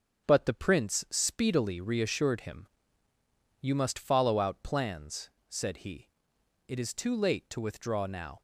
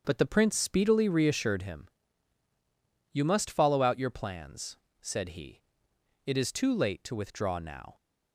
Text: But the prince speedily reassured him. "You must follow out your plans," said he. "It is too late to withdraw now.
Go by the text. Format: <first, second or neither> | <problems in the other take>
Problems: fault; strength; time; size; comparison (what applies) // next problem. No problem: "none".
second | starts louder than the rest; until 1.3 s; 7 dB; also in the second // skips "your"; at 4.6 s